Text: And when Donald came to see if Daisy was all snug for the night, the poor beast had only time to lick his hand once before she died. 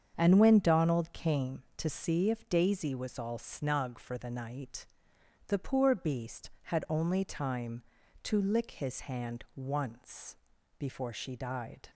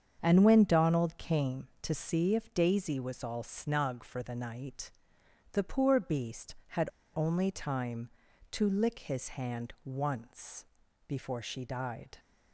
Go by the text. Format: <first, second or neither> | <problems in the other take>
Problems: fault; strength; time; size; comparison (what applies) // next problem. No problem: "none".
first | starts louder than the rest; strong; until 1.2 s; 7.5 dB; strong in the first // pauses between "had" and "only"; slight; at 6.9 s; 0.23 s long // pauses between "once" and "before"; at 10.6 s; 0.42 s long; also in the first